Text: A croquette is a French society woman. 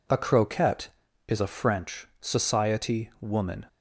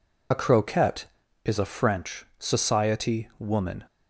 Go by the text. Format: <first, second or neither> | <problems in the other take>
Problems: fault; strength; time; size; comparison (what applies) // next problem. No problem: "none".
first | loses the start of "A"; at 0.3 s; 40 ms